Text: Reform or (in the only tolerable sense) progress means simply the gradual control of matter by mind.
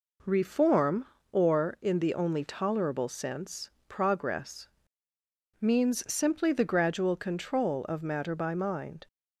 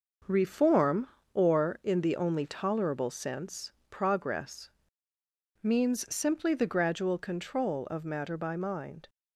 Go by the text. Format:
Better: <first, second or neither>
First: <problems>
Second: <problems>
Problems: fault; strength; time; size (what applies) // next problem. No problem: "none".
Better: first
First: pauses between "progress" and "means"; noticeable; at 4.6 s; 0.90 s long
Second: gets quieter; noticeable; throughout; 6 dB // pauses between "progress" and "means"; noticeable; at 4.7 s; 0.90 s long